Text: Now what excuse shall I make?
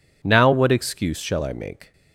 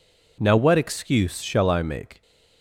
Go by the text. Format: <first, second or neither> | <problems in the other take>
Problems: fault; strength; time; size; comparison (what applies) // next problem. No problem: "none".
neither | none